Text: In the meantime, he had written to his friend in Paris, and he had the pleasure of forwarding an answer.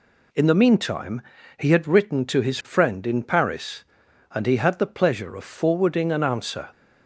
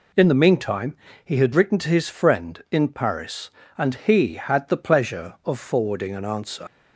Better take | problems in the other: first | leaves "answer" unfinished; at 6.6 s; 60 ms

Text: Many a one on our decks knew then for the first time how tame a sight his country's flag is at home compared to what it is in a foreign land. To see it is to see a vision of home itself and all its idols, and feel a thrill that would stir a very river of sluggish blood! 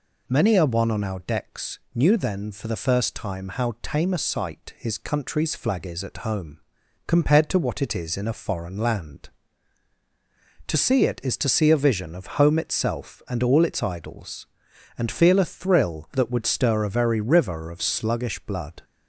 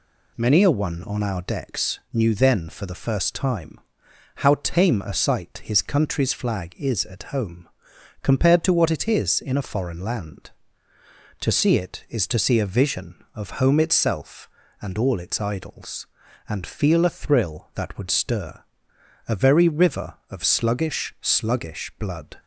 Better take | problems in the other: first | pauses between "time" and "how"; noticeable; at 3.7 s; 0.58 s long // pauses between "home" and "compared"; noticeable; at 7.6 s; 0.56 s long; noticeable in the first // pauses between "stir" and "a"; noticeable; at 18.6 s; 0.64 s long // says "sluggish" twice; at 21.2 s

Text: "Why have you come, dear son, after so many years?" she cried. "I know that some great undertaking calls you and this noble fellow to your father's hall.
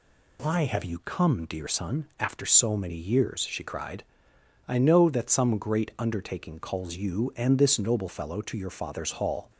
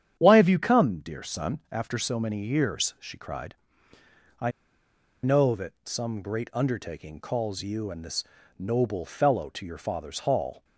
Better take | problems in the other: first | starts louder than the rest; strong; until 1.1 s; 9 dB // pauses between "I" and "know"; noticeable; at 4.5 s; 0.73 s long // pauses between "this" and "noble"; slight; at 8.2 s; 0.34 s long

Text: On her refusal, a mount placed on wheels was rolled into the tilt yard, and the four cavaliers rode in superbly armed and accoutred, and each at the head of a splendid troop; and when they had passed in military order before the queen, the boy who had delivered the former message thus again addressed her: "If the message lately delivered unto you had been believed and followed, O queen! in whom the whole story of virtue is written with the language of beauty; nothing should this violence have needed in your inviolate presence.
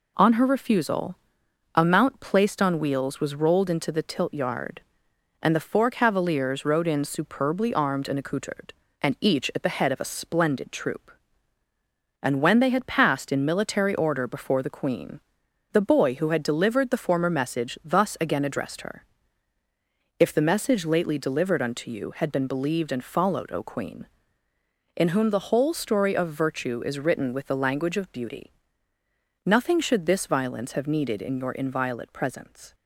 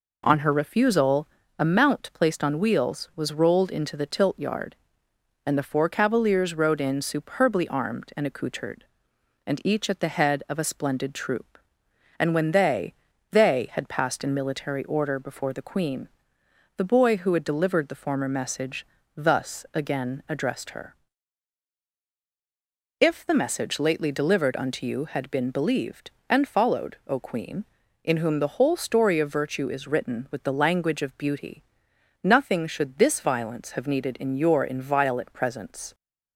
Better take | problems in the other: first | says "they" twice; at 13.3 s // pauses between "message" and "thus"; slight; at 18.8 s; 0.28 s long

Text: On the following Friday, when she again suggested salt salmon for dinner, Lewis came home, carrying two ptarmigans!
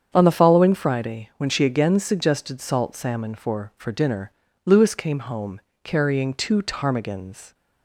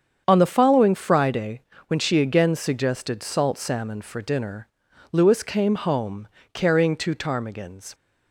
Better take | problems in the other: second | starts louder than the rest; strong; until 1.1 s; 8 dB; strong in the second // says "for" twice; at 3.7 s

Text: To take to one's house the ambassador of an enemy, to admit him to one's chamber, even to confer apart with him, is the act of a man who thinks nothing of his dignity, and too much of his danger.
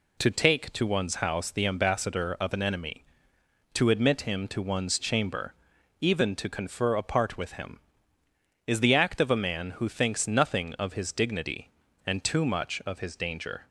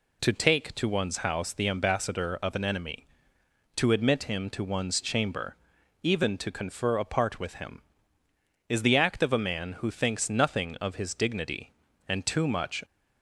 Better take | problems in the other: first | stops before "of his danger"; at 12.8 s

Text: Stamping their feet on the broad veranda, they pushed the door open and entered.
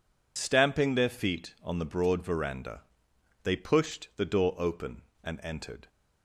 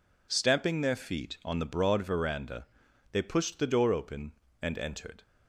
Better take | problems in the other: second | loses the start of "Stamping"; at 0.3 s; 50 ms

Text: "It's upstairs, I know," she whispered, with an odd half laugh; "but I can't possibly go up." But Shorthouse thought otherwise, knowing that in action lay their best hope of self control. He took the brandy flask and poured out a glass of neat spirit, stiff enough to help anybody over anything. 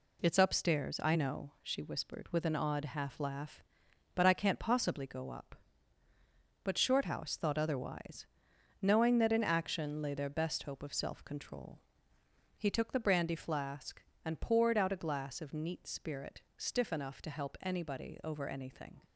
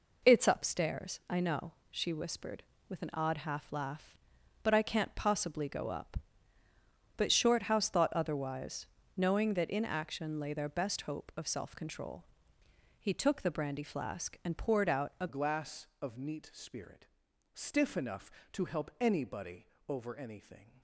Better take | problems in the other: first | changes voice at "glass"; from 15.2 s on; 5.6 s long // pauses between "anybody" and "over"; slight; at 19.6 s; 0.20 s long

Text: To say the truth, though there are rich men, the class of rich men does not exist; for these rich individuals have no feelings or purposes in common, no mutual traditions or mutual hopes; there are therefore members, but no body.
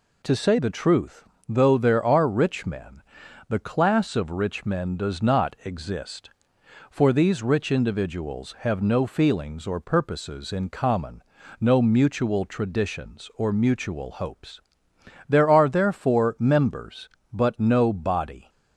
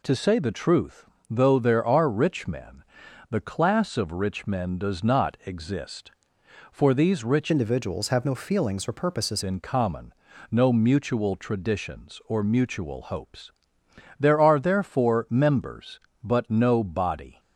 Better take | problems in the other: first | changes voice from "individuals" to "purposes"; from 7.4 to 9.4 s; 2.0 s long

